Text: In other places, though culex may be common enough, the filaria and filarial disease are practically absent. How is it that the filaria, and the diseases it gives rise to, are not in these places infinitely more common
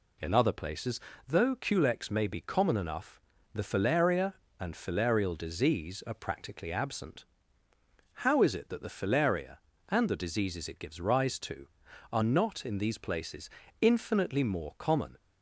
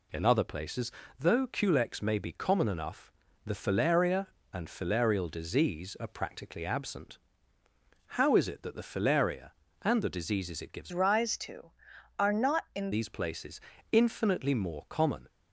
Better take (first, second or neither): first